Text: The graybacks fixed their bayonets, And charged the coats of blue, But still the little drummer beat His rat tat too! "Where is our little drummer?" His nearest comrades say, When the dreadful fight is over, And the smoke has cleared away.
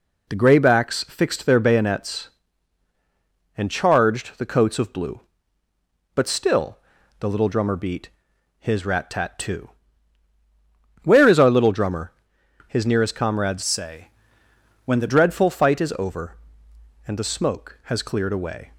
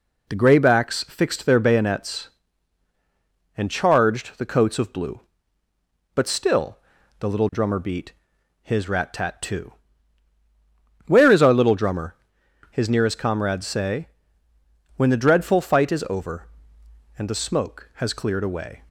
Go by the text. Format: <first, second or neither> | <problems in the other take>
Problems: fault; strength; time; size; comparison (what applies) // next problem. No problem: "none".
second | pauses between "still" and "the"; at 6.7 s; 0.42 s long; also in the second // pauses between "beat" and "His"; noticeable; at 8.0 s; 0.50 s long; noticeable in the second // changes voice from "say" to "the"; from 13.6 to 15.0 s; 1.4 s long